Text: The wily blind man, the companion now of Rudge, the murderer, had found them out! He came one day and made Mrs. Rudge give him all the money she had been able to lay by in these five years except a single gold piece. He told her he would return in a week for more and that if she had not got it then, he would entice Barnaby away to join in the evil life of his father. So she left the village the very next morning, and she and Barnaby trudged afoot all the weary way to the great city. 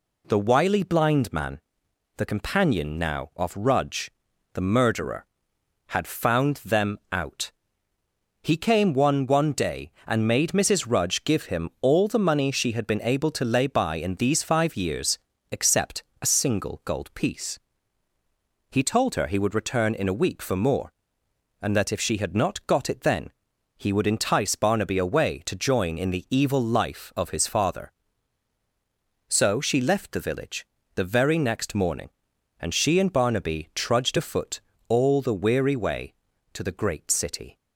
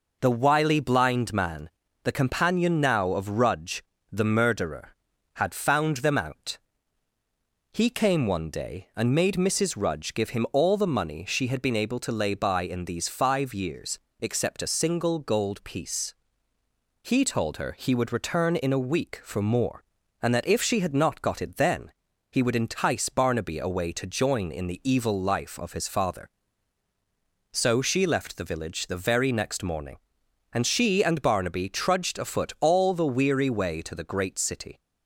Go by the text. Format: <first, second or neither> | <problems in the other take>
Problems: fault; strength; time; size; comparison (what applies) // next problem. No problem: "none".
second | says "one" twice; at 9.2 s // pauses between "years" and "except"; slight; at 15.1 s; 0.32 s long; slight in the second // pauses between "except" and "a"; slight; at 16.0 s; 0.22 s long // pauses between "village" and "the"; slight; at 30.6 s; 0.26 s long // pauses between "afoot" and "all"; slight; at 34.5 s; 0.28 s long